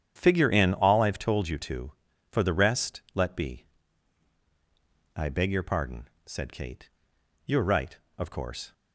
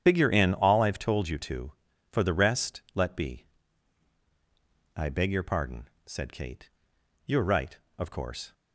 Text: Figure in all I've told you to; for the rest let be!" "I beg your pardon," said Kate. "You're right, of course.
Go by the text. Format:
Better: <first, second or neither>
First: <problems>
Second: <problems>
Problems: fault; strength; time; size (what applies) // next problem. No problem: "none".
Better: first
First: starts louder than the rest; strong; until 1.1 s; 9 dB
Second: loses the start of "Figure"; at 0.0 s; 100 ms // starts louder than the rest; strong; until 1.0 s; 9 dB